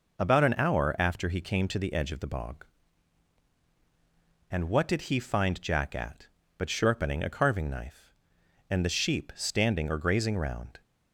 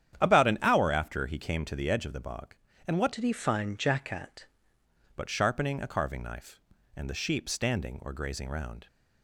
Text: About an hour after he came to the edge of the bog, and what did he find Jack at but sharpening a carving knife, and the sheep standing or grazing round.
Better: first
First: none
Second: starts louder than the rest; strong; until 1.2 s; 10 dB // changes voice from "did" to "at"; from 3.1 to 4.4 s; 1.3 s long

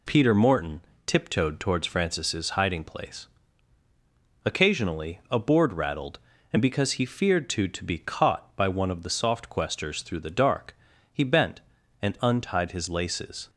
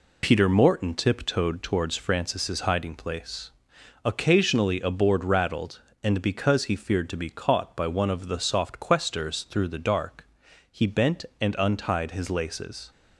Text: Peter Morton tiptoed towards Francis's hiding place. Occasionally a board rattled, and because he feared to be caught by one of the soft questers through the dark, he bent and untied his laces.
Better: second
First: pauses between "Morton" and "tiptoed"; slight; at 0.7 s; 0.26 s long // says "to" twice; at 7.6 s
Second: none

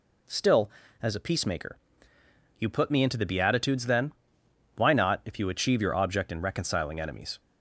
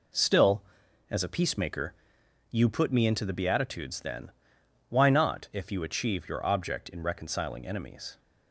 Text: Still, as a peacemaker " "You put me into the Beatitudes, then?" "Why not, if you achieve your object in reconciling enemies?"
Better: neither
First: none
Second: none

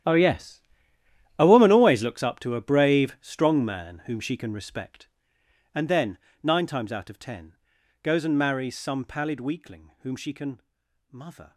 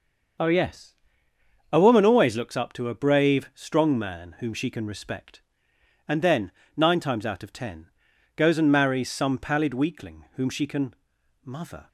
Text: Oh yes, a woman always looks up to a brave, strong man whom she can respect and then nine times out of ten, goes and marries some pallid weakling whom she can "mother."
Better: second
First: gets quieter; strong; throughout; 16 dB // starts louder than the rest; strong; until 1.8 s; 11 dB // pauses between "then" and "nine"; slight; at 6.1 s; 0.22 s long // pauses between "can" and "mother"; noticeable; at 10.6 s; 0.50 s long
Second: starts louder than the rest; until 2.1 s; 6 dB // pauses between "then" and "nine"; slight; at 6.5 s; 0.22 s long // pauses between "can" and "mother"; noticeable; at 10.9 s; 0.50 s long

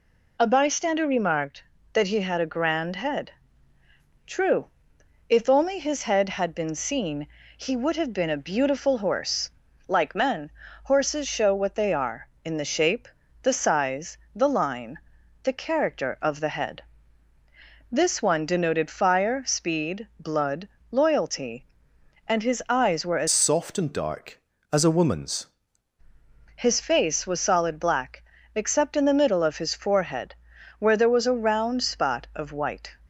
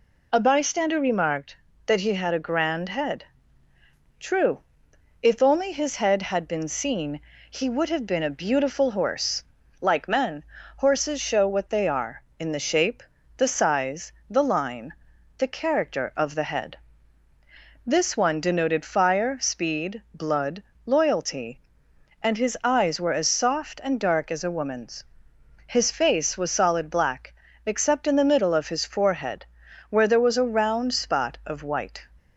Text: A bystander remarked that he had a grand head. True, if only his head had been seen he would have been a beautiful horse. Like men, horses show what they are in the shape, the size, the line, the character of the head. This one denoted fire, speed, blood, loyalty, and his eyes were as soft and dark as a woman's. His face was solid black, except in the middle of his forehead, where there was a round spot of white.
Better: second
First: pauses between "seen" and "he"; slight; at 7.2 s; 0.28 s long // changes voice from "soft" to "woman's"; from 23.2 to 25.4 s; 2.2 s long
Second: pauses between "seen" and "he"; slight; at 7.2 s; 0.28 s long

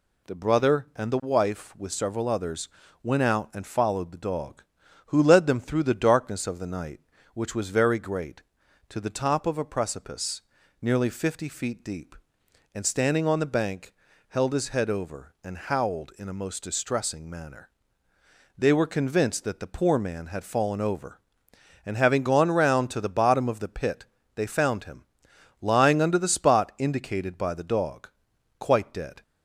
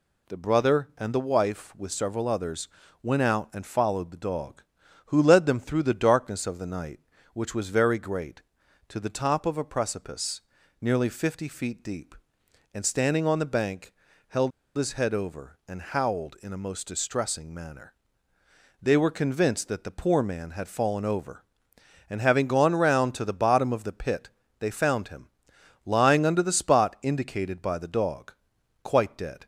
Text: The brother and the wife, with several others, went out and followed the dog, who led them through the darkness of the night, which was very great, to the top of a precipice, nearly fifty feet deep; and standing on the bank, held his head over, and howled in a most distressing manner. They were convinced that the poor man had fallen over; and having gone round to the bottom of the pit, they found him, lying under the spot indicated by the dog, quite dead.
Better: first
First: none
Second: pauses between "held" and "his"; slight; at 14.5 s; 0.25 s long

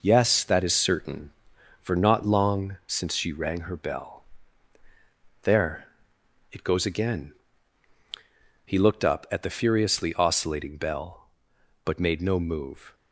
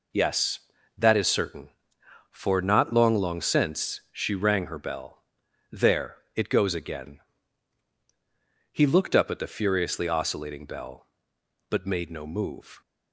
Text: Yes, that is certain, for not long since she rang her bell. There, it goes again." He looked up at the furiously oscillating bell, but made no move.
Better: first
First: none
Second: says "long" twice; at 3.1 s

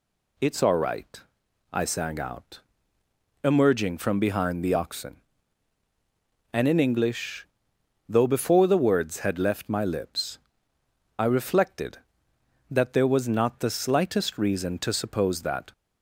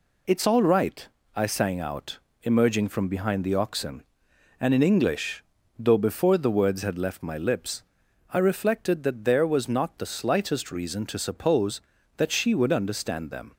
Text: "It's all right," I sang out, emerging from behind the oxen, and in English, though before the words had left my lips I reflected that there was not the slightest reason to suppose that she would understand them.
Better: second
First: pauses between "lips" and "I"; noticeable; at 10.3 s; 0.80 s long // stops before "she would understand them"; at 15.7 s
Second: pauses between "lips" and "I"; noticeable; at 7.8 s; 0.50 s long

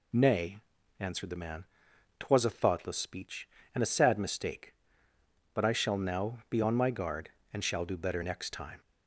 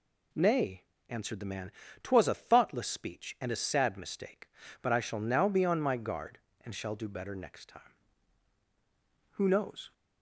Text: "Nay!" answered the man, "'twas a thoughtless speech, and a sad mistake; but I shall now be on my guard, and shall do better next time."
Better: first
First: none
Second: goes on to say "Who knows"; from 9.3 s on; 0.58 s long

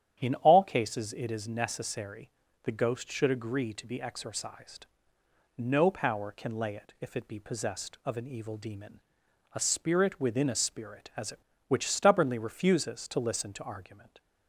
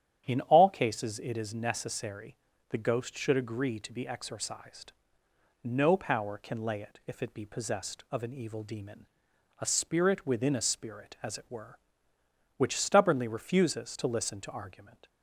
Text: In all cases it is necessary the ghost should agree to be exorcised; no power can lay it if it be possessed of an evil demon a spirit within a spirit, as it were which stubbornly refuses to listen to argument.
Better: second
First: starts louder than the rest; strong; until 1.2 s; 10.5 dB // pauses between "necessary" and "the"; slight; at 2.2 s; 0.34 s long // pauses between "demon" and "a"; noticeable; at 8.9 s; 0.54 s long // skips "were"; at 11.5 s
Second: starts louder than the rest; strong; until 1.2 s; 10.5 dB // pauses between "necessary" and "the"; slight; at 2.3 s; 0.34 s long // pauses between "demon" and "a"; noticeable; at 9.0 s; 0.54 s long

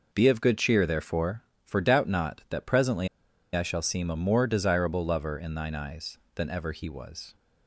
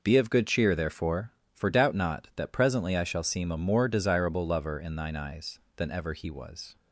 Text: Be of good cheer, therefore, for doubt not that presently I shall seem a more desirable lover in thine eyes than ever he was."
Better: second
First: pauses between "presently" and "I"; noticeable; at 3.0 s; 0.46 s long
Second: none

